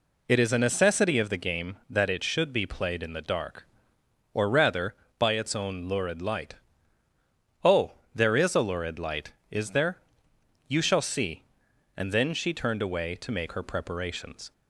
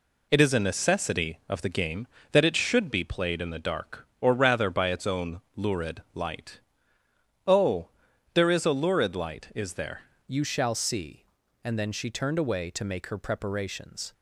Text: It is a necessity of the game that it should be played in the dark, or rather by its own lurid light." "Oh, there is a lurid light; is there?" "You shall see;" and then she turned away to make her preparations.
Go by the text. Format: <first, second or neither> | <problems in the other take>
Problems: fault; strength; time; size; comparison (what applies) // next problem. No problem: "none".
first | pauses between "own" and "lurid"; slight; at 5.4 s; 0.16 s long // changes voice at "You"; from 10.2 s on; 3.9 s long